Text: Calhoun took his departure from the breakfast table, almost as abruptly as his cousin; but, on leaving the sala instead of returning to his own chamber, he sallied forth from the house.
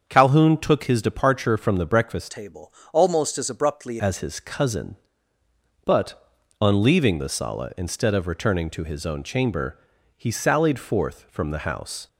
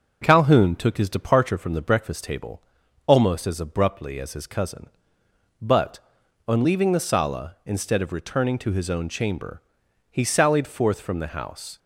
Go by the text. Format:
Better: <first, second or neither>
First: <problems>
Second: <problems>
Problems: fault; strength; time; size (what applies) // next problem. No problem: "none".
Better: second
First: starts louder than the rest; until 1.0 s; 7 dB // changes voice from "table" to "abruptly"; from 2.2 to 3.9 s; 1.7 s long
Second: none